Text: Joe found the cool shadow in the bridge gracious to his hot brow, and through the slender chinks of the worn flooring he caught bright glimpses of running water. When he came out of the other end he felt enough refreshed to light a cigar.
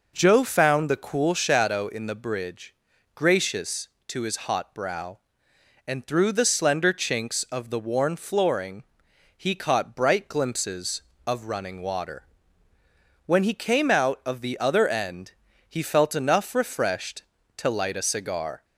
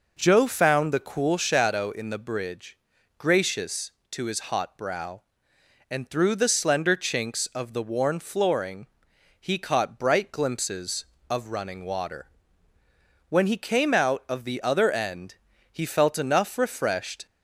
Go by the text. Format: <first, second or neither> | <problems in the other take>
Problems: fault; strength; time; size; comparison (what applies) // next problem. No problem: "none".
first | pauses between "bridge" and "gracious"; at 2.7 s; 0.44 s long; also in the first // pauses between "flooring" and "he"; noticeable; at 8.8 s; 0.52 s long; noticeable in the first // pauses between "end" and "he"; slight; at 15.3 s; 0.36 s long; slight in the first // stops before "to light a cigar"; at 17.2 s